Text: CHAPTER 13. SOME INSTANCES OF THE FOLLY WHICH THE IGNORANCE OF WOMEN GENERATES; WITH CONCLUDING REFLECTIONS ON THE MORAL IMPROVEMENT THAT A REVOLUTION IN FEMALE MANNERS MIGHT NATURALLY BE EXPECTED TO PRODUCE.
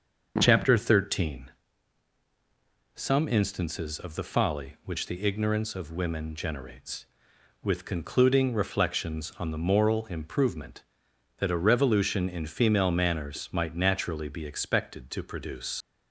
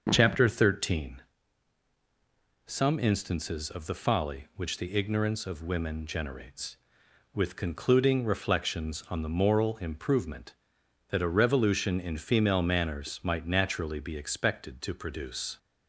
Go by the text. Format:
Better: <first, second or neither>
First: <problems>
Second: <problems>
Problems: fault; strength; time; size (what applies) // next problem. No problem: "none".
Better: second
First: starts louder than the rest; until 1.3 s; 6.5 dB // leaves "PRODUCE" unfinished; at 15.8 s; 60 ms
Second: starts louder than the rest; until 1.1 s; 6.5 dB